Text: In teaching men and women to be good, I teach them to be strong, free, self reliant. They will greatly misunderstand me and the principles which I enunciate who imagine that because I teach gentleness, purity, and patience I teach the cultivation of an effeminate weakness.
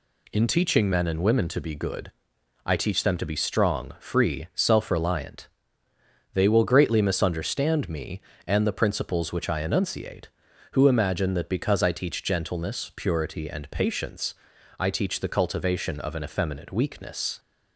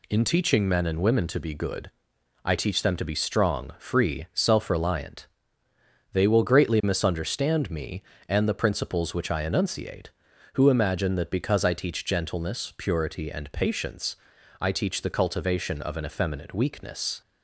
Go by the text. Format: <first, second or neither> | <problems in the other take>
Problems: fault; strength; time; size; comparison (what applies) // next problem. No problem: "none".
neither | pauses between "patience" and "I"; the same in both